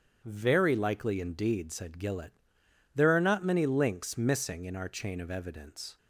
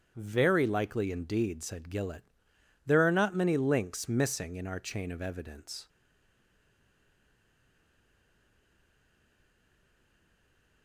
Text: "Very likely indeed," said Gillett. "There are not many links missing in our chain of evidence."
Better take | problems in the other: first | starts louder than the rest; strong; until 1.1 s; 8.5 dB; strong in the first // stays silent after the last word; strong; from 5.8 s on; 5.0 s long

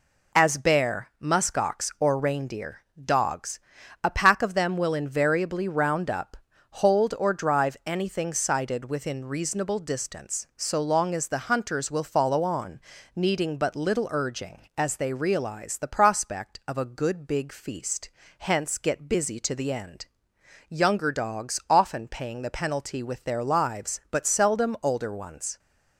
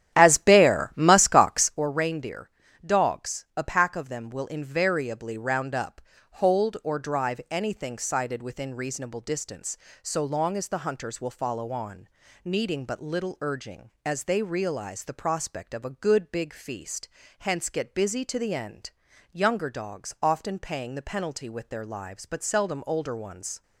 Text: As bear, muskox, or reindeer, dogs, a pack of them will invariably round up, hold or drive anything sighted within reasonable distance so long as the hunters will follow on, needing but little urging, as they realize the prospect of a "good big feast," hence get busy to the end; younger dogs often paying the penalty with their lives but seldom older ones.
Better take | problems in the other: first | starts louder than the rest; strong; until 1.8 s; 11 dB

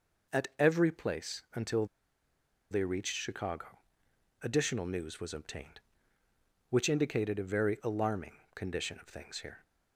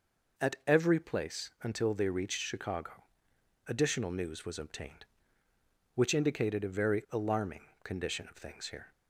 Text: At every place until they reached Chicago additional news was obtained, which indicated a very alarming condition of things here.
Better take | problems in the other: second | pauses between "until" and "they"; noticeable; at 1.8 s; 0.84 s long // pauses between "Chicago" and "additional"; noticeable; at 3.7 s; 0.64 s long; noticeable in the second // pauses between "alarming" and "condition"; slight; at 8.3 s; 0.22 s long; slight in the second

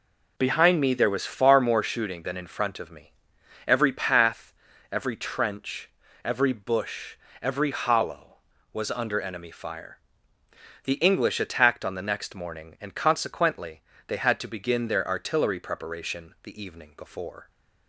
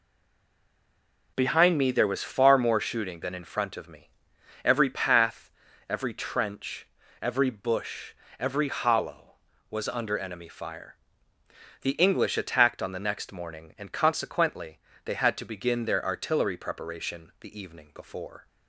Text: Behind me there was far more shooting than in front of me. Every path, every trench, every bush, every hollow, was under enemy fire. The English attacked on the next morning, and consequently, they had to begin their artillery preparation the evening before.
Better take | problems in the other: first | stays silent before the first word; noticeable; until 1.3 s; 1.3 s long

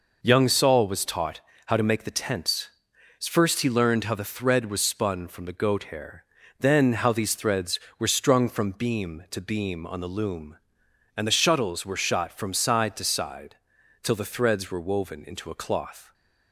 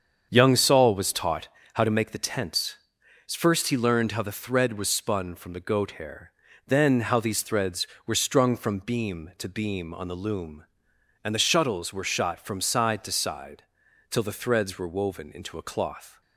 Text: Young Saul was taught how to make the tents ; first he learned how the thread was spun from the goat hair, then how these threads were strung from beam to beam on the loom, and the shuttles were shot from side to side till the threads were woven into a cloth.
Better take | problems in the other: first | starts louder than the rest; strong; until 1.9 s; 7.5 dB // pauses between "taught" and "how"; slight; at 1.4 s; 0.24 s long; slight in the first // pauses between "side" and "till"; noticeable; at 13.6 s; 0.48 s long; noticeable in the first

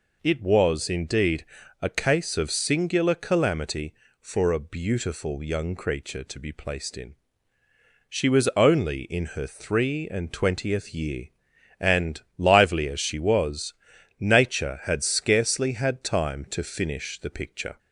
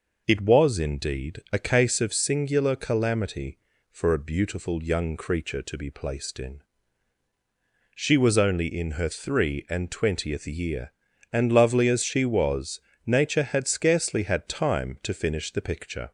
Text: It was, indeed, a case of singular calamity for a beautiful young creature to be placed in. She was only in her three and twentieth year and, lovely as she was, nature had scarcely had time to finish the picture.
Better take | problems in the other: second | says "lively" for "lovely"; at 12.3 s

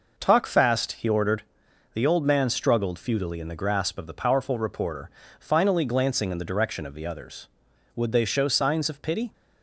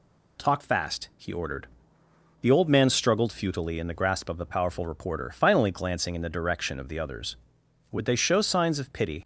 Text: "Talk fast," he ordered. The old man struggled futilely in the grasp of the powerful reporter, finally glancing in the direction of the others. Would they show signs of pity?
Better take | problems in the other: neither | none

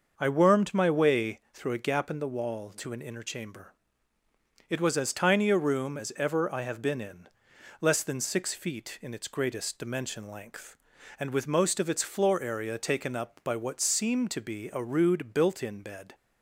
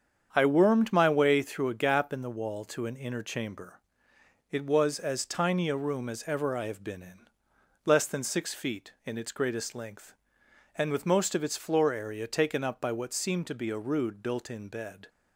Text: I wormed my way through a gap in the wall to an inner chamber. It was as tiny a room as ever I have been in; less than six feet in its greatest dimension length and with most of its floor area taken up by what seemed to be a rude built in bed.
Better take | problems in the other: first | starts louder than the rest; strong; until 1.3 s; 7.5 dB; also in the first // skips "dimension"; at 9.7 s

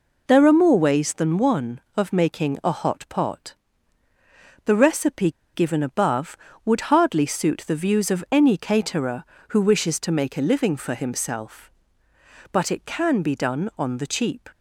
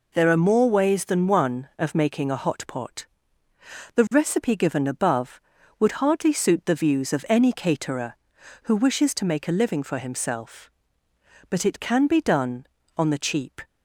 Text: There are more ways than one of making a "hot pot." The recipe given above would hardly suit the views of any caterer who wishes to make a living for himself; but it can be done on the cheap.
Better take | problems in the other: second | pauses between "recipe" and "given"; slight; at 5.3 s; 0.21 s long

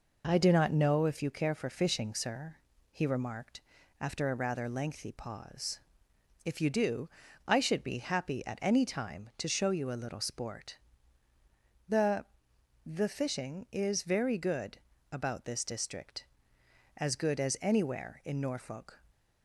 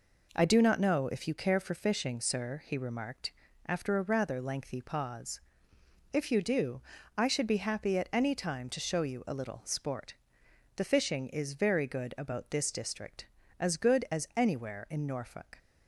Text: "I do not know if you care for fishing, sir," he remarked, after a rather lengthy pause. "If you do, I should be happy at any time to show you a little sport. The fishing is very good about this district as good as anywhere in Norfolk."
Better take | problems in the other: second | says "The" twice; at 12.8 s // pauses between "good" and "about"; slight; at 14.7 s; 0.32 s long

